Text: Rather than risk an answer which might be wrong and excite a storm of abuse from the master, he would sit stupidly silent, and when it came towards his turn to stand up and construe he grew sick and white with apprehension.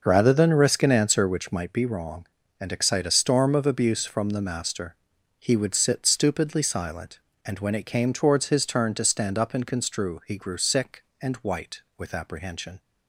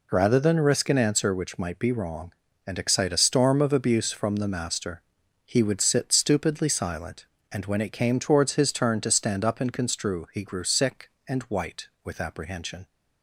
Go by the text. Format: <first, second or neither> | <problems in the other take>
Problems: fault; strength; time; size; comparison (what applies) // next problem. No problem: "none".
second | starts louder than the rest; noticeable; until 1.7 s; 5.5 dB